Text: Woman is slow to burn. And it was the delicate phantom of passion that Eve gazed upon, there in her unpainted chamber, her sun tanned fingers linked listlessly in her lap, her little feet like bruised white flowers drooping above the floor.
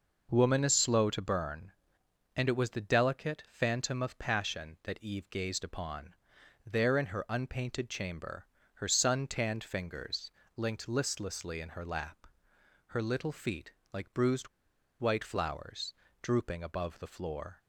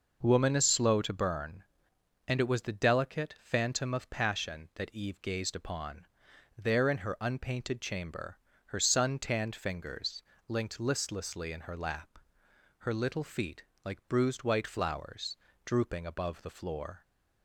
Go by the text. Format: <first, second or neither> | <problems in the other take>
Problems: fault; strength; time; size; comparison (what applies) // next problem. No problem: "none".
second | pauses between "fingers" and "linked"; slight; at 10.2 s; 0.26 s long; slight in the second // pauses between "feet" and "like"; slight; at 13.7 s; 0.20 s long; slight in the second // pauses between "bruised" and "white"; noticeable; at 14.4 s; 0.51 s long // pauses between "flowers" and "drooping"; slight; at 15.9 s; 0.30 s long; slight in the second